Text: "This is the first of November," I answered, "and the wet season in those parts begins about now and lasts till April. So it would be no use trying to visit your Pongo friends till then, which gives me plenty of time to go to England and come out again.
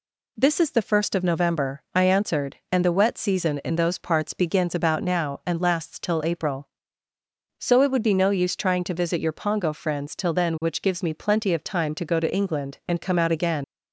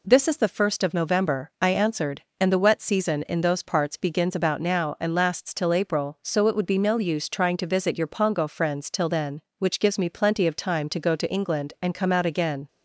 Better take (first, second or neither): second